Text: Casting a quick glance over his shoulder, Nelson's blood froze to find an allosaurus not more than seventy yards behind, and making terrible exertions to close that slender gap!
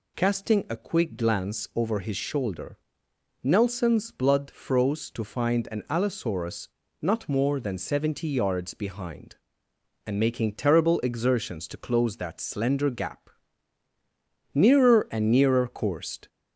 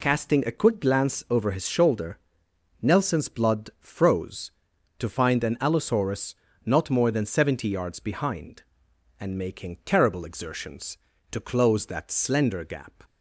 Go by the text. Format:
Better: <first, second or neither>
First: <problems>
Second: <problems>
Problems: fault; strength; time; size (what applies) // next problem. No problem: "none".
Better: second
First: pauses between "allosaurus" and "not"; slight; at 6.6 s; 0.34 s long // goes on to say "Nearer and nearer coursed"; strong; from 14.5 s on; 1.7 s long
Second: pauses between "allosaurus" and "not"; slight; at 6.3 s; 0.32 s long